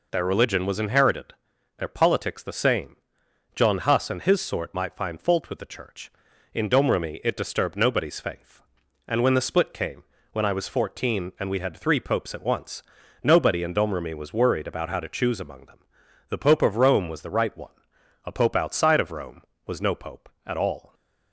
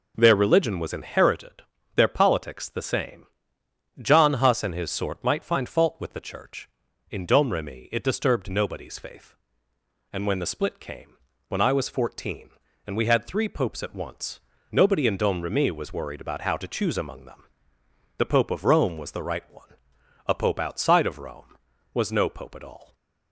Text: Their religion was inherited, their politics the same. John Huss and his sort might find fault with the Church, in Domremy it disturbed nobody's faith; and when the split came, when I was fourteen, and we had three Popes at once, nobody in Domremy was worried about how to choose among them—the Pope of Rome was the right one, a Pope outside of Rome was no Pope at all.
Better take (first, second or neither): neither